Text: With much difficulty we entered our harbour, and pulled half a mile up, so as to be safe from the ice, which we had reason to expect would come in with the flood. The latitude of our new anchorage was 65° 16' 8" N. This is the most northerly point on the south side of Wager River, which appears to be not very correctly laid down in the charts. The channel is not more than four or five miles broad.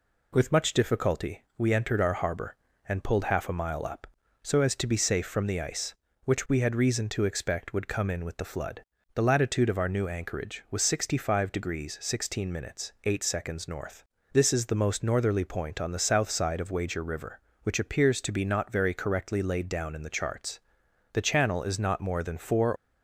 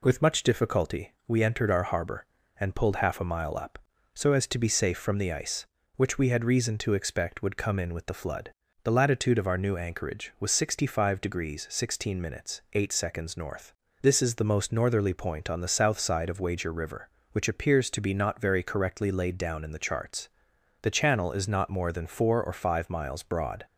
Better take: second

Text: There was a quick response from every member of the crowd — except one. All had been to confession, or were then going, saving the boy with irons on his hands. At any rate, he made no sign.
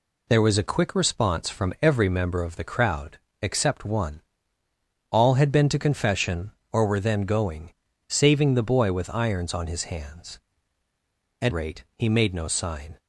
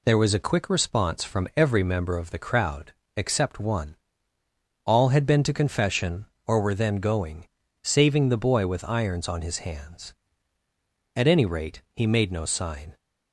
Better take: second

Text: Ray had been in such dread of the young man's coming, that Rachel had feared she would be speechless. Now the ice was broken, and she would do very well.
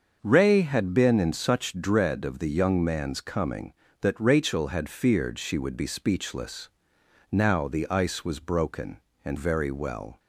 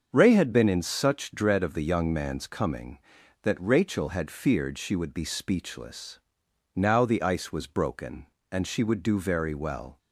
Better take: second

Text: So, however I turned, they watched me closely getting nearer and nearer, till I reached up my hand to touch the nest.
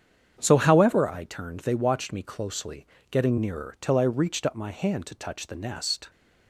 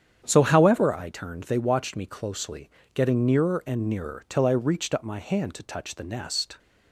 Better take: second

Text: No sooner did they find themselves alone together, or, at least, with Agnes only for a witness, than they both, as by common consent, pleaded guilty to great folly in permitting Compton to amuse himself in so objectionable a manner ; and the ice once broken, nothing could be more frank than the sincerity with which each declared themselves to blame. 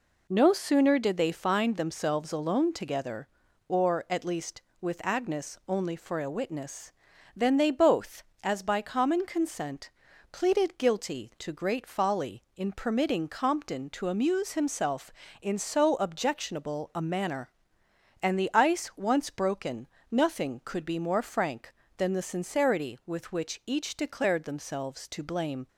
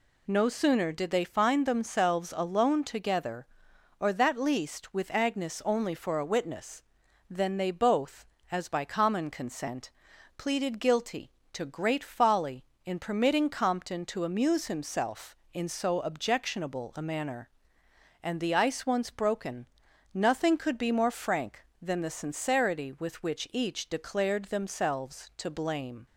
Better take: first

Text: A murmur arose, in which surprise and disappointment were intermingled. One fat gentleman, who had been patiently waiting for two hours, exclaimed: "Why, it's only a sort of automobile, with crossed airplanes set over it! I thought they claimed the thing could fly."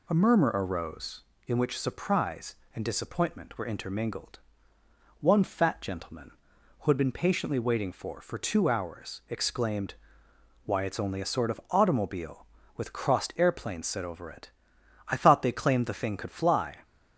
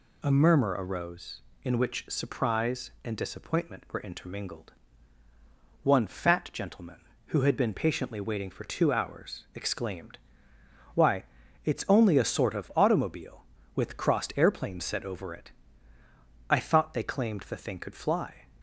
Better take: second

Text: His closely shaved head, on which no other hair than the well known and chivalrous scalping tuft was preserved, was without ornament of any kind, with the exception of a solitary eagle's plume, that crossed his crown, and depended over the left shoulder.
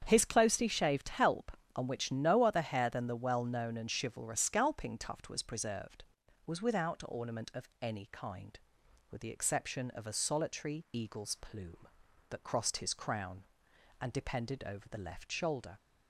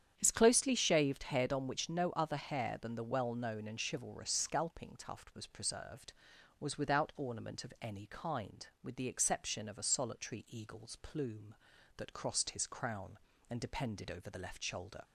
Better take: second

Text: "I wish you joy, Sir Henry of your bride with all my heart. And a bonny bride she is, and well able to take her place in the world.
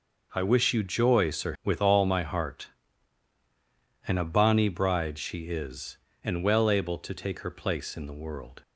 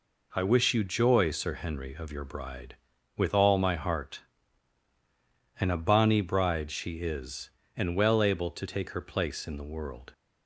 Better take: second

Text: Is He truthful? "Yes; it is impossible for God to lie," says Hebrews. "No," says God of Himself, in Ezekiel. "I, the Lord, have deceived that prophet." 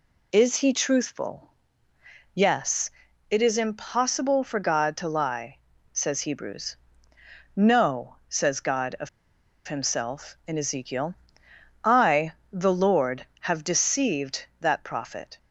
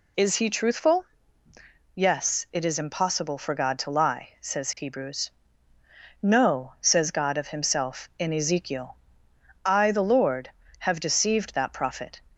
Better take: second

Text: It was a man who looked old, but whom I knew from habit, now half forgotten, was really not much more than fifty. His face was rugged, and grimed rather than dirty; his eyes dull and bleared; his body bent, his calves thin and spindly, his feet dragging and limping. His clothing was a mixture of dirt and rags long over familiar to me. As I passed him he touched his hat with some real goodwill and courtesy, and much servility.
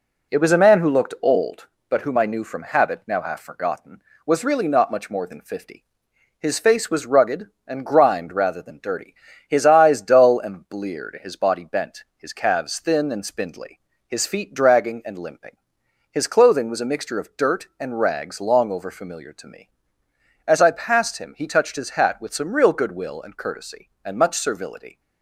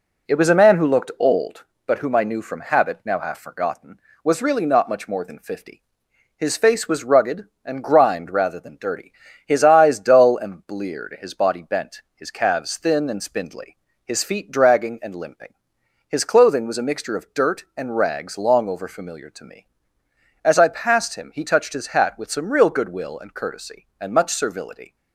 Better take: neither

